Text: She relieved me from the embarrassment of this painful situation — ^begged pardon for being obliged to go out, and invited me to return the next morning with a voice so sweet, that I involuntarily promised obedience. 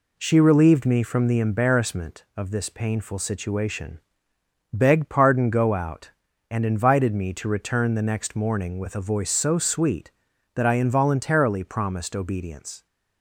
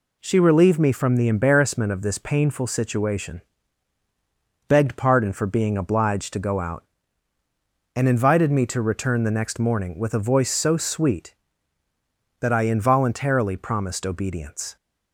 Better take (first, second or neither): second